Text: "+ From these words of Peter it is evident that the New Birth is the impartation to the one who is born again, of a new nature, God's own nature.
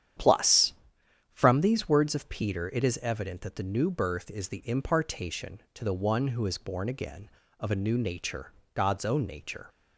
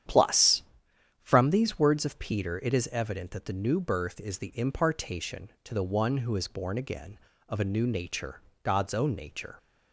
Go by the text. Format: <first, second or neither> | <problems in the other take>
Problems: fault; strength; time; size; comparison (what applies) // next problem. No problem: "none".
neither | starts louder than the rest; strong; the same in both